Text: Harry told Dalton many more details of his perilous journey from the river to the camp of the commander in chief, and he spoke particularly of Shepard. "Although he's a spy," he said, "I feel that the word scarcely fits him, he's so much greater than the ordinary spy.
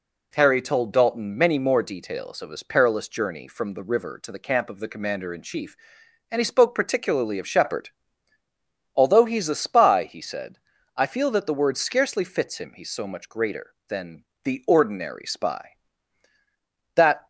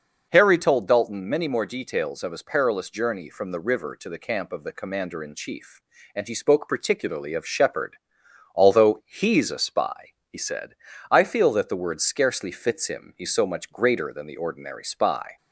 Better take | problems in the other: second | pauses between "than" and "the"; slight; at 14.2 s; 0.20 s long // goes on to say "That"; slight; from 16.9 s on; 0.32 s long

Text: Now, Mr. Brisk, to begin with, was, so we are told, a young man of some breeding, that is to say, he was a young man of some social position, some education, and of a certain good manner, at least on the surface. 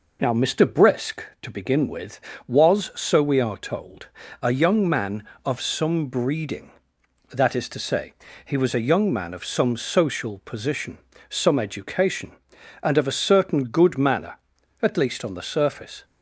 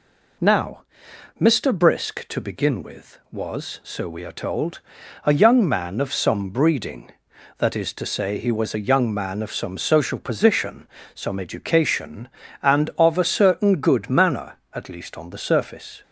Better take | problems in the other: neither | none

